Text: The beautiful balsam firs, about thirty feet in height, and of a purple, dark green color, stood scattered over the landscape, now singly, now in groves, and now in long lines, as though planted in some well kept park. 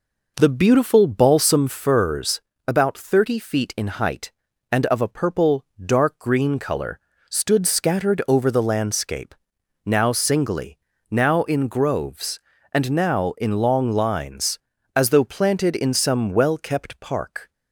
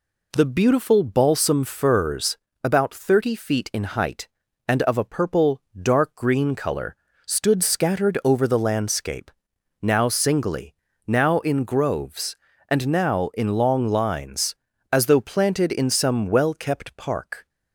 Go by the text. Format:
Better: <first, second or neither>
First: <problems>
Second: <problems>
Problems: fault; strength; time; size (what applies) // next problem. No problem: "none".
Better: second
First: starts louder than the rest; noticeable; until 1.7 s; 5 dB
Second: none